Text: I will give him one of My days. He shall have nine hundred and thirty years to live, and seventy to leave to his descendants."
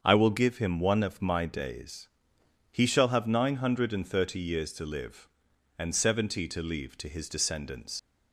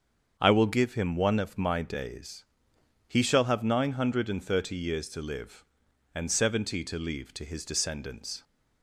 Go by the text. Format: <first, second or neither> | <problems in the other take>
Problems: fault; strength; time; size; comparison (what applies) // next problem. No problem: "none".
second | starts louder than the rest; until 1.0 s; 7 dB; also in the second // leaves "descendants" unfinished; at 7.9 s; 75 ms